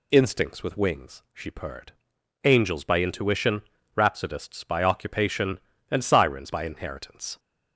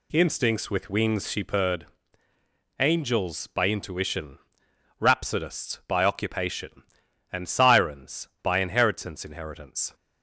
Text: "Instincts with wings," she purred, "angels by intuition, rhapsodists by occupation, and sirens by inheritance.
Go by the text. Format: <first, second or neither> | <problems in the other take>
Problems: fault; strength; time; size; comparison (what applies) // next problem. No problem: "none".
first | says "inheritance" twice; at 9.2 s